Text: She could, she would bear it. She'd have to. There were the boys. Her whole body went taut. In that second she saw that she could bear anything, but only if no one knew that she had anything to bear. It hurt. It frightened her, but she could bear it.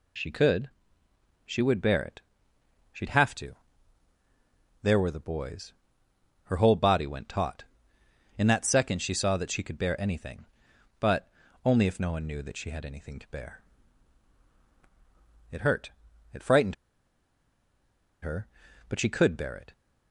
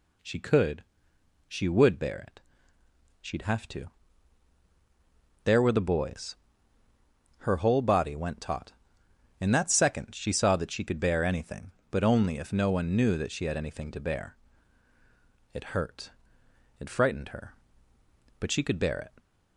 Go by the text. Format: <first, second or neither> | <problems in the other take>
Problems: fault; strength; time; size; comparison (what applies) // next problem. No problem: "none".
second | pauses between "but" and "only"; at 11.2 s; 0.38 s long // pauses between "frightened" and "her"; strong; at 16.7 s; 1.4 s long